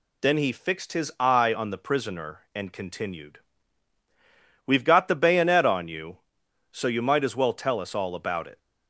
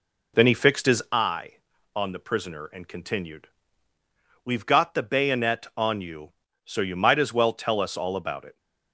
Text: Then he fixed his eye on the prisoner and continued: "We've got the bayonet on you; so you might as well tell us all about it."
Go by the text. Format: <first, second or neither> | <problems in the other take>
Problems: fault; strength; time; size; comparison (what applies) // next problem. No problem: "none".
first | starts louder than the rest; noticeable; until 1.2 s; 4 dB